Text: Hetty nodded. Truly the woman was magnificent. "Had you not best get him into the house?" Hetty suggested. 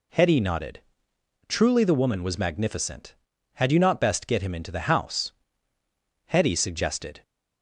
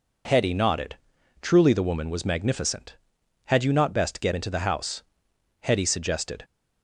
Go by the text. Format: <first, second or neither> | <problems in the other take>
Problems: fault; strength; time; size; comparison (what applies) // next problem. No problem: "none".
first | skips "him"; at 4.3 s